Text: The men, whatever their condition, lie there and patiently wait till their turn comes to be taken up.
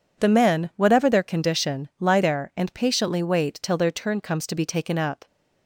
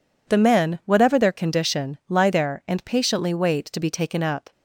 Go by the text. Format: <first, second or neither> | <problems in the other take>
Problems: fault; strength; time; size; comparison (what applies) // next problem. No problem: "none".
first | skips "till their turn comes"; at 3.7 s